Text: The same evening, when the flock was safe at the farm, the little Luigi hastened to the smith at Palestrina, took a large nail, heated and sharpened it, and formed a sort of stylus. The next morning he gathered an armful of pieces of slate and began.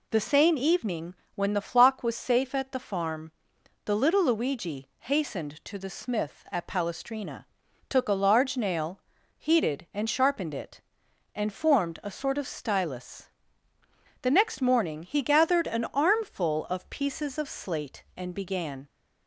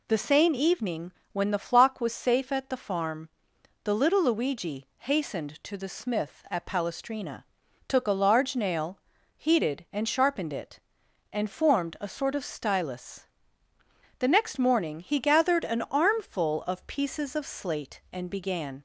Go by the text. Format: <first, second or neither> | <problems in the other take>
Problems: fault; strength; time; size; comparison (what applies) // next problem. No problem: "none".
neither | none